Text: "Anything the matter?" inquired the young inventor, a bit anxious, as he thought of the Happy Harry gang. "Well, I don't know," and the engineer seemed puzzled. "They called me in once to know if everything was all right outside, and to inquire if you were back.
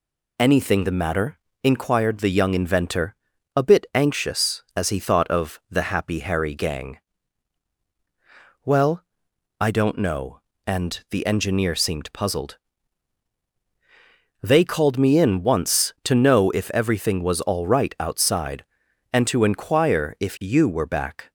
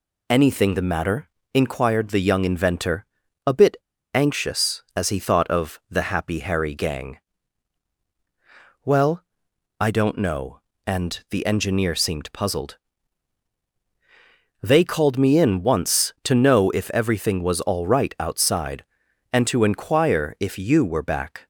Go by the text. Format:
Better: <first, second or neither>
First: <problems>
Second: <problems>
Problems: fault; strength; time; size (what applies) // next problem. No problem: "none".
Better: first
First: none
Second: pauses between "bit" and "anxious"; at 3.7 s; 0.37 s long